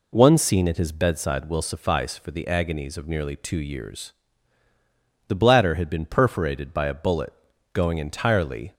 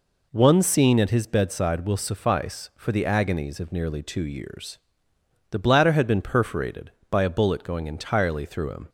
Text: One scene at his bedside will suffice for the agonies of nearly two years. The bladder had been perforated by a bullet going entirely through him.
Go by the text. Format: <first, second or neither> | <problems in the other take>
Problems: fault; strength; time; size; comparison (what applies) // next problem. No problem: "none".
second | pauses between "bullet" and "going"; at 7.3 s; 0.40 s long // stops before "through him"; at 8.7 s